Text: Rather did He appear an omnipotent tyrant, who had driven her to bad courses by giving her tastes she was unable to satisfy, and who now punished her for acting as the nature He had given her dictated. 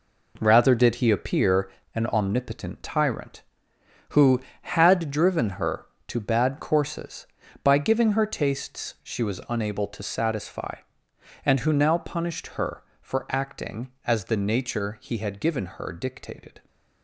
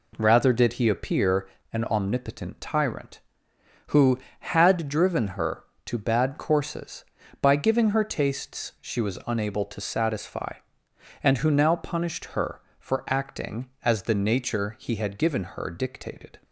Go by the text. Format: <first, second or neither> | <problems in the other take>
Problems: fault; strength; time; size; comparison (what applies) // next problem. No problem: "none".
second | gets quieter; strong; throughout; 8 dB // pauses between "appear" and "an"; slight; at 1.7 s; 0.24 s long; slight in the second